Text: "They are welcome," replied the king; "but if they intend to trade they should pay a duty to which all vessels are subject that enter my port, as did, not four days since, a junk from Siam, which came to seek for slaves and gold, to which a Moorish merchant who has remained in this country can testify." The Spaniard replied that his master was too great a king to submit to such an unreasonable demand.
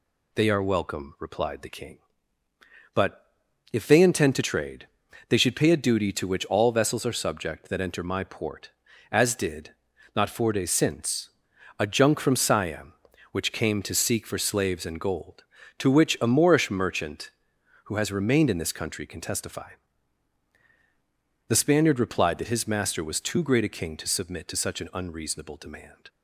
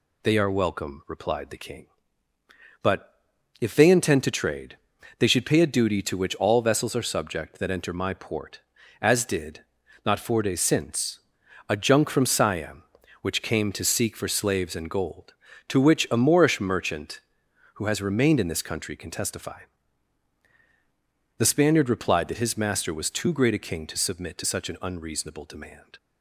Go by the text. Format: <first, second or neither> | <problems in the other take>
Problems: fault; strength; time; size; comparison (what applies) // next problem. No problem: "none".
neither | pauses between "but" and "if"; the same in both // pauses between "trade" and "they"; the same in both